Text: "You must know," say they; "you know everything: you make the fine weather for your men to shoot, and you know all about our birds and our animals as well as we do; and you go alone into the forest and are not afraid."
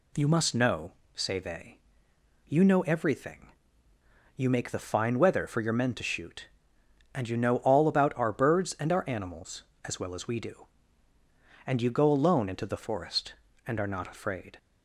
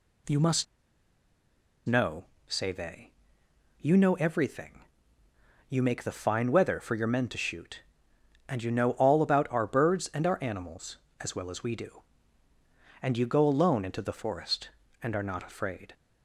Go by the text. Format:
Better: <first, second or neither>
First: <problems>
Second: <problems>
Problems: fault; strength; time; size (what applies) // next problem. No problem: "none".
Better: first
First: none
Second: pauses between "must" and "know"; at 0.6 s; 1.2 s long